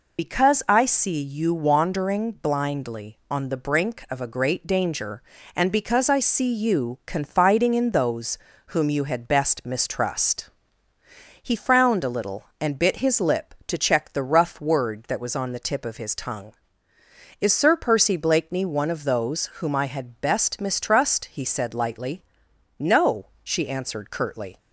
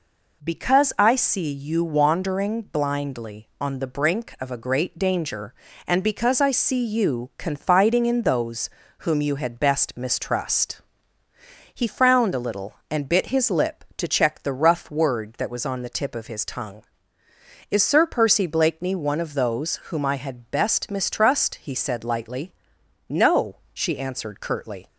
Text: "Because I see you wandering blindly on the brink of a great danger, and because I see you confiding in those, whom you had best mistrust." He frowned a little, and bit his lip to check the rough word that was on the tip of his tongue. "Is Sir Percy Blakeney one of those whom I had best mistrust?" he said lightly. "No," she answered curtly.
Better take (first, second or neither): second